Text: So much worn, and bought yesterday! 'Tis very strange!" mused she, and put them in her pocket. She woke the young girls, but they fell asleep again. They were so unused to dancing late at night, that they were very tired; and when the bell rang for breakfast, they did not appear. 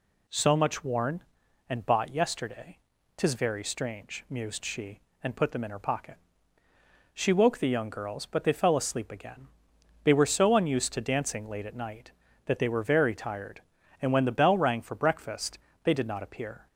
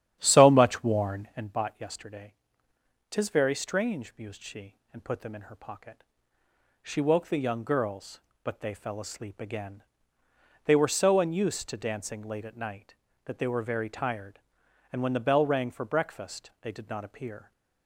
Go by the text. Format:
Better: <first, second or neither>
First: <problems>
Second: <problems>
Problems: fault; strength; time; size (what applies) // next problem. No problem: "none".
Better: first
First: none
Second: starts louder than the rest; strong; until 1.5 s; 10.5 dB